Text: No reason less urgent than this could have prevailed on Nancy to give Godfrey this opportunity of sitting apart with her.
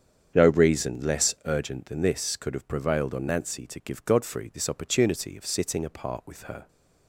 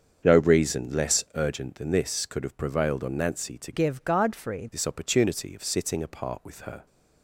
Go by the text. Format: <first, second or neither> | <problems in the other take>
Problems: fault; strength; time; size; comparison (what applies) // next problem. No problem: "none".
first | starts louder than the rest; until 1.3 s; 7 dB; strong in the first // changes voice from "give" to "Godfrey"; from 3.7 to 4.6 s; 0.9 s long